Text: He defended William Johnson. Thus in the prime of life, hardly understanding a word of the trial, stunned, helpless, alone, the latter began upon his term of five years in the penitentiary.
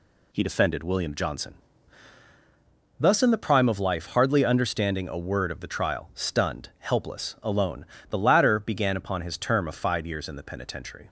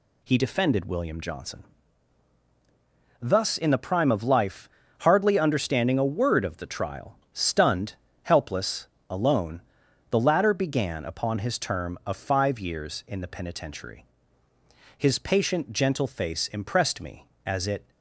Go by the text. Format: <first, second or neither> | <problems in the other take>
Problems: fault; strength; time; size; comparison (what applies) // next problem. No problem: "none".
first | goes on to say "His patient gentle face impressed me as it"; strong; from 14.9 s on; 2.9 s long